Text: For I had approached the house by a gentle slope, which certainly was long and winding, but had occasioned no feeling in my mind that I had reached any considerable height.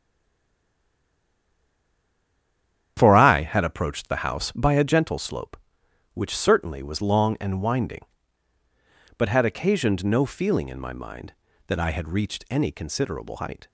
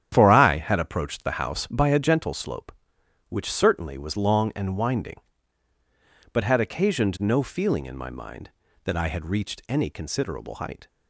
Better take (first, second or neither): second